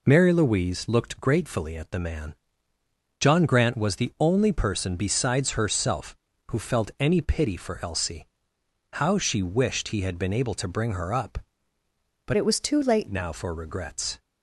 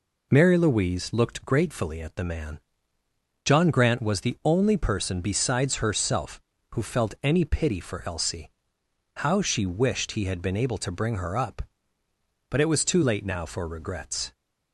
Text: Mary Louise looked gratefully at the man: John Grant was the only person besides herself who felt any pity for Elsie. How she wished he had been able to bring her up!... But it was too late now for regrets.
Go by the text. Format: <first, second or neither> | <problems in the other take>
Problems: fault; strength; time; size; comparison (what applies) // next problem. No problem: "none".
second | changes voice from "it" to "late"; from 12.3 to 13.0 s; 0.7 s long